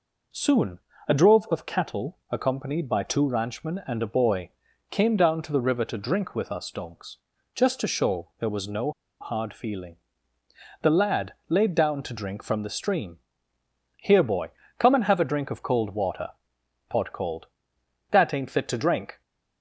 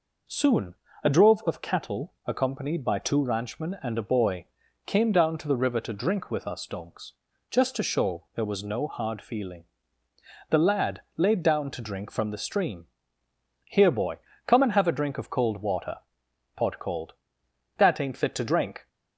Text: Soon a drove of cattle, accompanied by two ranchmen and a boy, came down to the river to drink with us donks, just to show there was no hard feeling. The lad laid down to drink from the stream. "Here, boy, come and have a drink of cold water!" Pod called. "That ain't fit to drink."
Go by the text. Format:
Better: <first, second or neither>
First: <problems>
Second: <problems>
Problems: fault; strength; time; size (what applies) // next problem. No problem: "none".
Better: second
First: pauses between "Soon" and "a"; slight; at 0.7 s; 0.28 s long // pauses between "no" and "hard"; slight; at 8.9 s; 0.29 s long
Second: pauses between "Soon" and "a"; slight; at 0.7 s; 0.28 s long